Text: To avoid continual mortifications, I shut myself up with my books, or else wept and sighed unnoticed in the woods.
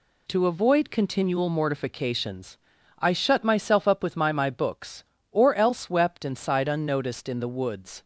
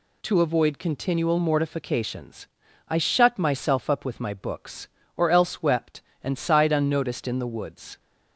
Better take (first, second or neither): second